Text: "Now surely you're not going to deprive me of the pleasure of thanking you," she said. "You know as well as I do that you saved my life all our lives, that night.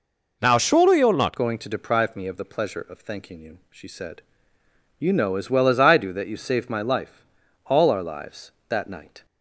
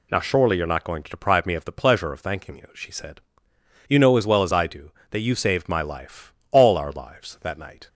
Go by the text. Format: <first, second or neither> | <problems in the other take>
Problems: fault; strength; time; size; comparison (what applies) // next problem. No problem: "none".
second | changes voice at "going"; from 1.3 s on; 7.9 s long // pauses between "life" and "all"; at 7.2 s; 0.44 s long; slight in the second